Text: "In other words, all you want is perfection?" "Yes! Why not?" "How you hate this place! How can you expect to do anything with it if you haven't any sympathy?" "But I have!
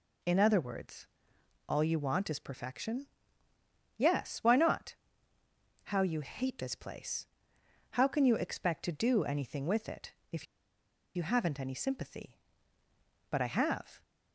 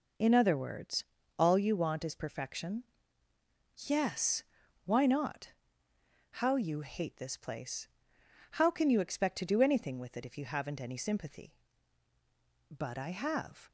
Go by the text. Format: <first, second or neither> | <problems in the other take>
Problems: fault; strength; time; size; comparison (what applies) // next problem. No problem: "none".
second | pauses between "it" and "if"; slight; at 10.1 s; 0.18 s long // pauses between "if" and "you"; noticeable; at 10.4 s; 0.70 s long